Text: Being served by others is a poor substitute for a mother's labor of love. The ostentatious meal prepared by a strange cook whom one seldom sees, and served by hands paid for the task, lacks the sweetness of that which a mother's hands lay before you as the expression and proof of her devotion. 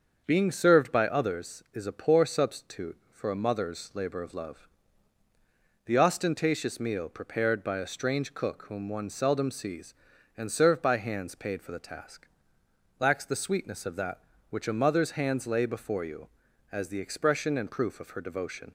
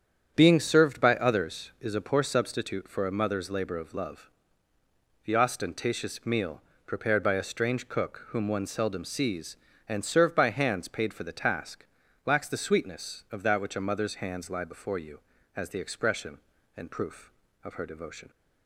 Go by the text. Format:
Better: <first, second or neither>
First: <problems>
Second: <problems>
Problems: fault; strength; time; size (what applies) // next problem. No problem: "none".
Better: first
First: starts louder than the rest; until 1.2 s; 6.5 dB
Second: starts louder than the rest; strong; until 1.3 s; 8.5 dB // pauses between "meal" and "prepared"; slight; at 6.5 s; 0.28 s long // says "lie" for "lay"; at 14.4 s